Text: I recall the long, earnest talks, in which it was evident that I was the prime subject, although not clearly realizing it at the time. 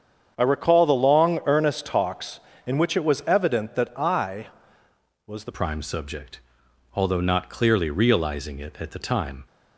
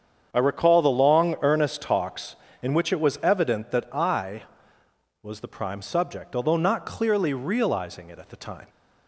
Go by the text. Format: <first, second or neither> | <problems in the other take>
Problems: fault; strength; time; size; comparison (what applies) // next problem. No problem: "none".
second | starts louder than the rest; strong; until 1.3 s; 7.5 dB; strong in the second // changes voice at "prime"; from 5.5 s on; 3.9 s long